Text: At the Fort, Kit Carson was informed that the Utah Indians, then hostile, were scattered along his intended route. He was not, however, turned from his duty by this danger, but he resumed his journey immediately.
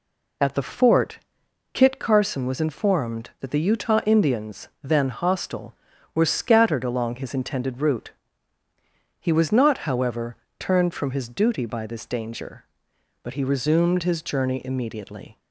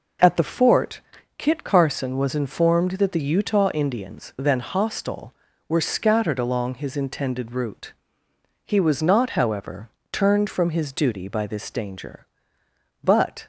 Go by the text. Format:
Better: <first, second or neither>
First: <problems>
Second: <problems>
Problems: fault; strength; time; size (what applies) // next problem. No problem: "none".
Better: first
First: none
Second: stops before "he resumed his journey immediately"; at 13.4 s